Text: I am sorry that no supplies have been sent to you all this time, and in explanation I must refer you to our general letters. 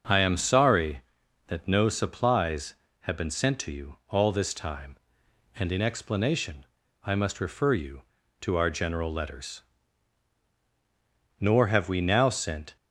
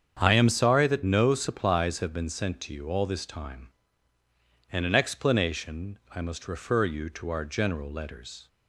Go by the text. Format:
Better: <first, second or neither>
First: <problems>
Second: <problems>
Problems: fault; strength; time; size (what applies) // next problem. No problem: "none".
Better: second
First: starts louder than the rest; until 1.5 s; 6.5 dB // pauses between "explanation" and "I"; at 6.6 s; 0.40 s long // goes on to say "Nor have we now sent"; from 11.3 s on; 1.3 s long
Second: starts louder than the rest; strong; until 1.2 s; 7.5 dB